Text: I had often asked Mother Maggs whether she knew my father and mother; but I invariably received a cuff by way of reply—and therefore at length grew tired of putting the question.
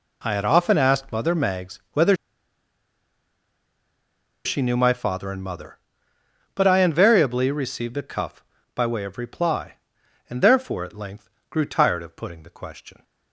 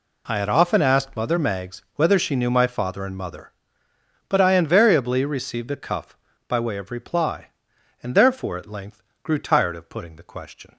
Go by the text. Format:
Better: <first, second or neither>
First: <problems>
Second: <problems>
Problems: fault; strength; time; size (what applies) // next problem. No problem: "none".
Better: second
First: pauses between "whether" and "she"; strong; at 2.1 s; 2.3 s long // pauses between "length" and "grew"; slight; at 11.2 s; 0.20 s long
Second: pauses between "length" and "grew"; slight; at 9.0 s; 0.20 s long